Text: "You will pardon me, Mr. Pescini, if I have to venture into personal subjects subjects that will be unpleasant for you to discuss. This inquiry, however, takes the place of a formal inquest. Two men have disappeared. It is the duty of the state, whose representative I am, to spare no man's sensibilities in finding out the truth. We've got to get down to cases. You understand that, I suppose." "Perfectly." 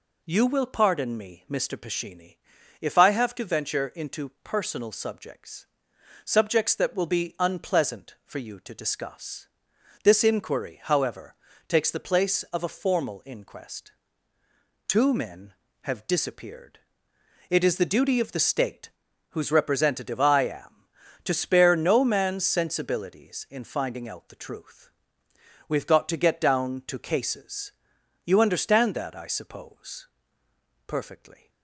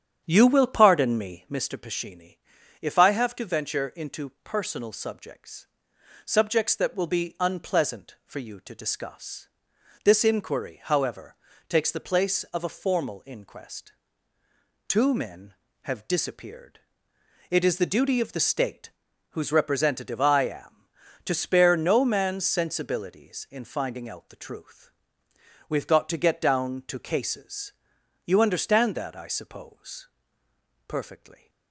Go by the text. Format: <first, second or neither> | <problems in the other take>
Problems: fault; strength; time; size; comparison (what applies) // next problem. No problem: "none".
first | starts louder than the rest; strong; until 1.5 s; 8.5 dB // pauses between "into" and "personal"; slight; at 4.2 s; 0.16 s long; slight in the first // pauses between "subjects" and "subjects"; noticeable; at 5.6 s; 0.58 s long; noticeable in the first